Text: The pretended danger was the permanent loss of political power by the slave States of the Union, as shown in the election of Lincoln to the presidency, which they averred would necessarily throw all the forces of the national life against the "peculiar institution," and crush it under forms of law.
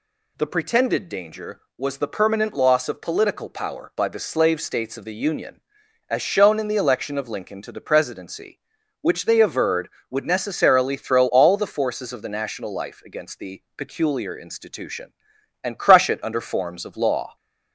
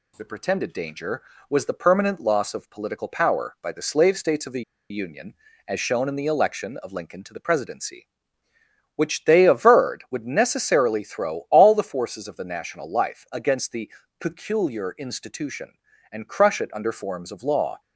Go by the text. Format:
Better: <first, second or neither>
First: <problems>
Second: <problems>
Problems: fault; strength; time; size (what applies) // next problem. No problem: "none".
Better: first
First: none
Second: pauses between "the" and "Union"; slight; at 4.6 s; 0.28 s long // pauses between "the" and "peculiar"; slight; at 13.9 s; 0.26 s long